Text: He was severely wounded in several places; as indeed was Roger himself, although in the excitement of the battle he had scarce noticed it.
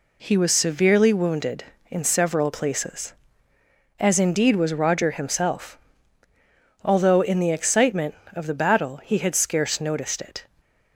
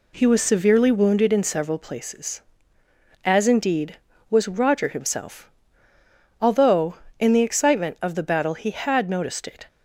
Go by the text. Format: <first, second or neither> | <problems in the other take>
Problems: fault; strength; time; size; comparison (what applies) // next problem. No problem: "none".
first | skips "scarce"; at 9.1 s